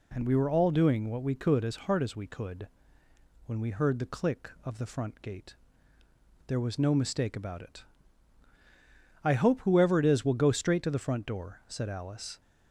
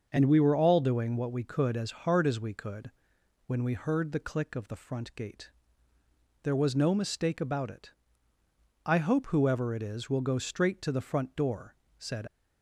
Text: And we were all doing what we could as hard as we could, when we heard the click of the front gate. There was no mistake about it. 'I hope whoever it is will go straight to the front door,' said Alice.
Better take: first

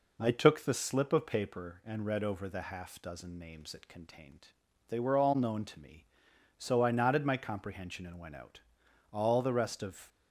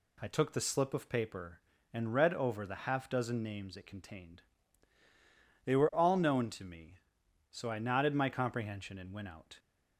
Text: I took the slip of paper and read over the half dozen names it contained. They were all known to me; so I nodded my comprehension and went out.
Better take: second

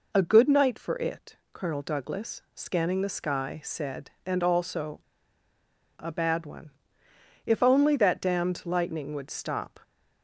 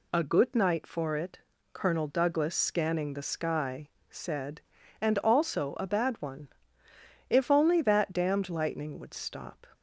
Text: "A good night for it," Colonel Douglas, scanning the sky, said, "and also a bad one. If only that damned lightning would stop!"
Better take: second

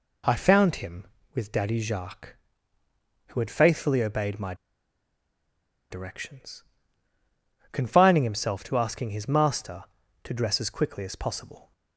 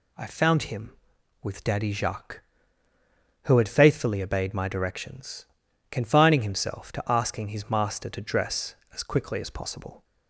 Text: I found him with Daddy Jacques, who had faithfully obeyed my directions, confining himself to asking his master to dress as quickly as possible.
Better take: second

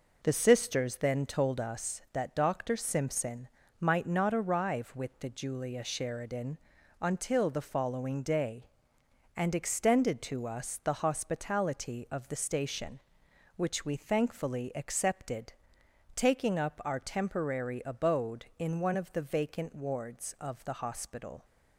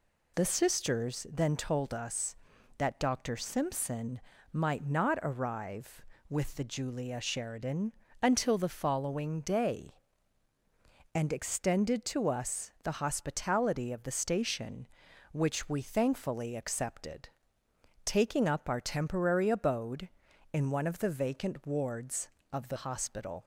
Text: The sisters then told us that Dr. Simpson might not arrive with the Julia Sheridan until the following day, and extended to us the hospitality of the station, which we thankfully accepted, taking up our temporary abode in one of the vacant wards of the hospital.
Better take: second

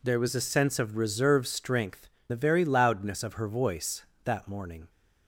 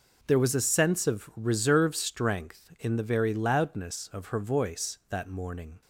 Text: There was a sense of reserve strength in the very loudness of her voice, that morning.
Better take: second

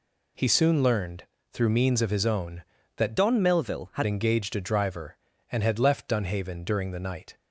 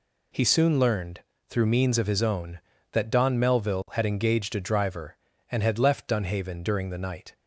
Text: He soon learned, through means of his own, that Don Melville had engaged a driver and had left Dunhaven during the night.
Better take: second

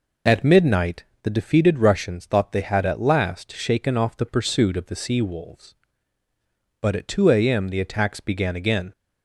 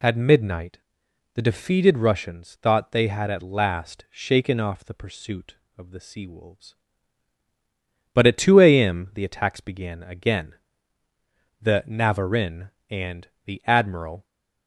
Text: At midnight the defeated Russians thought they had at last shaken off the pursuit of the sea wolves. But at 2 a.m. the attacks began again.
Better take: first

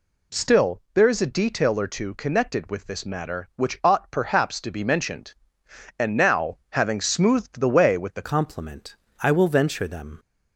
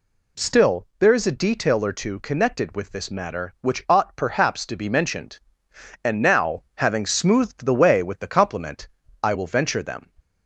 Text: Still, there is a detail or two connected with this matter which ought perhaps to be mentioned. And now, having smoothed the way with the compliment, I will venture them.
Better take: second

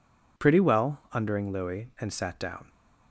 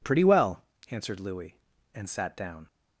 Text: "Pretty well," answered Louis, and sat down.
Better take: second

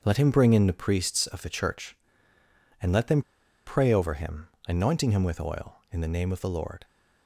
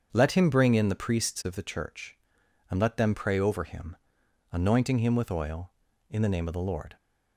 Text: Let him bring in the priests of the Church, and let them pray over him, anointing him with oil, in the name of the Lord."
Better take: second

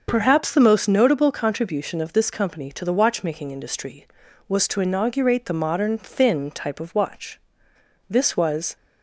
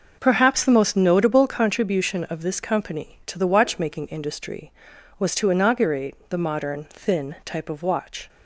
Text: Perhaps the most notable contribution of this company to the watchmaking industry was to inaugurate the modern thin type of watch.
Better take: second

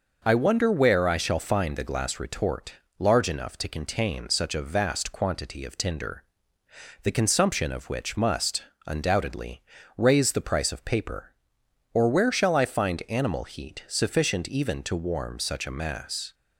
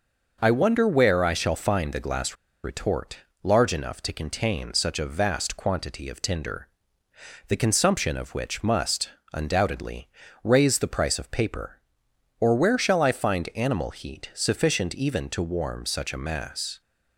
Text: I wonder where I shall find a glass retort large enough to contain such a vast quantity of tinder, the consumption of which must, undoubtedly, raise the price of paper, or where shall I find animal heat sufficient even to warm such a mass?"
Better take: first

